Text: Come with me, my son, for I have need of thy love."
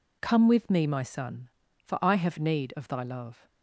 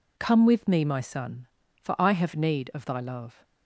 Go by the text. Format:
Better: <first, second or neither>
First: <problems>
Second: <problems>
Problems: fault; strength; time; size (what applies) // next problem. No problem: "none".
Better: neither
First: none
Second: none